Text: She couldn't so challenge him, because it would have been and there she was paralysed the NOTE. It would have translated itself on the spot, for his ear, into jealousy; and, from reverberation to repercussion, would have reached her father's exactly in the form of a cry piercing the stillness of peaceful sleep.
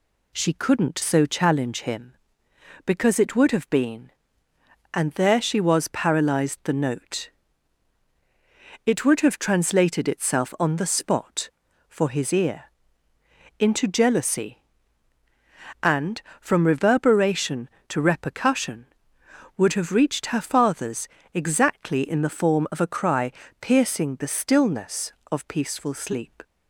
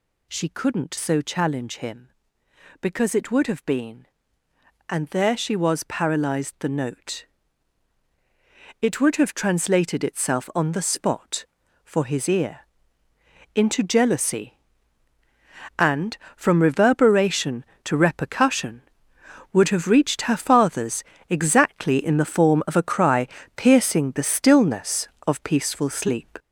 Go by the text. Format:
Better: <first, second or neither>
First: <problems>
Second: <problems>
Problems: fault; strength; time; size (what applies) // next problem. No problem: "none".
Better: first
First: pauses between "father's" and "exactly"; slight; at 21.0 s; 0.26 s long // pauses between "cry" and "piercing"; slight; at 23.3 s; 0.28 s long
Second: gets louder; throughout; 6.5 dB // pauses between "father's" and "exactly"; slight; at 21.0 s; 0.26 s long // pauses between "cry" and "piercing"; slight; at 23.2 s; 0.28 s long